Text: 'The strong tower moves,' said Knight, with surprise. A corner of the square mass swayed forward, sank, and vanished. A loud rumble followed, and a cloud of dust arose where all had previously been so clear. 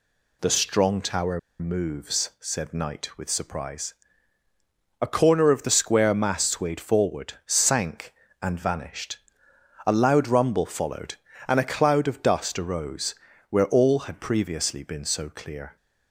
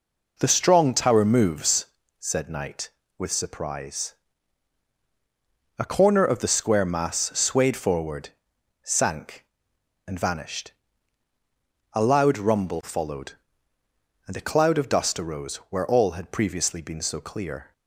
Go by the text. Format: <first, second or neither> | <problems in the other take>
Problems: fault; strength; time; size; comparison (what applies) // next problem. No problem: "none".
second | pauses between "tower" and "moves"; slight; at 1.3 s; 0.21 s long // pauses between "arose" and "where"; slight; at 13.1 s; 0.34 s long